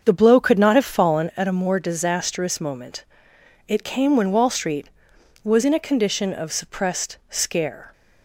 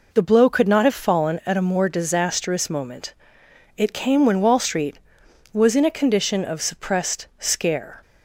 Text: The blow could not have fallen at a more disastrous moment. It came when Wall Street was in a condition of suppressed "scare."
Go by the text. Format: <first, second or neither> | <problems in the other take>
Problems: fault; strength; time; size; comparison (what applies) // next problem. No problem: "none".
second | starts louder than the rest; until 1.4 s; 7 dB